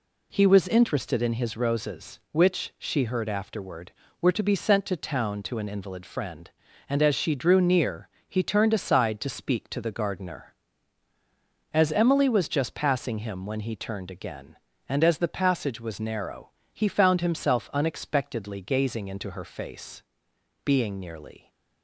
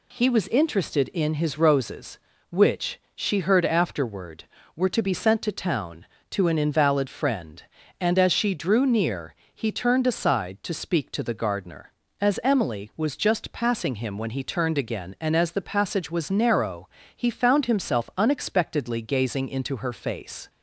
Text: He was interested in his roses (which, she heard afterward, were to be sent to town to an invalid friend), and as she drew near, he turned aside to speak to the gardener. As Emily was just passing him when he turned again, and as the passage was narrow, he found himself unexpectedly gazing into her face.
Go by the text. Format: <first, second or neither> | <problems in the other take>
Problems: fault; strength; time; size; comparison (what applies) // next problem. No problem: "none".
second | goes on to say "Being nearly"; noticeable; from 20.6 s on; 0.86 s long